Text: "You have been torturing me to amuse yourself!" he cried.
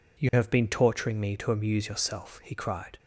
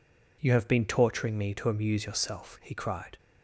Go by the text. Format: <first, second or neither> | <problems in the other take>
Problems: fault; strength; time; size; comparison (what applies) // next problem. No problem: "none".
neither | none